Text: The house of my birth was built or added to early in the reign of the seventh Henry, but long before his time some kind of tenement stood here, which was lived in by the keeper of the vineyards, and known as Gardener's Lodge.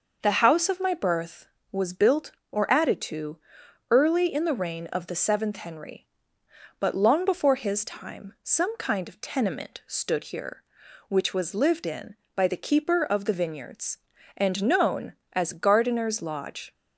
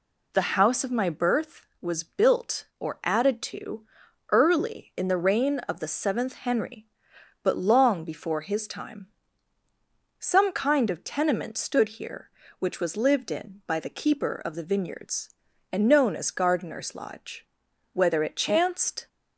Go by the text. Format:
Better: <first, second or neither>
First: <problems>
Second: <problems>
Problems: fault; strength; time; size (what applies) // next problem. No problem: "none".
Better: first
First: pauses between "to" and "early"; noticeable; at 3.3 s; 0.54 s long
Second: pauses between "to" and "early"; noticeable; at 3.8 s; 0.48 s long // pauses between "time" and "some"; at 9.0 s; 1.1 s long // goes on to say "Whether it chanced"; noticeable; from 17.9 s on; 1.1 s long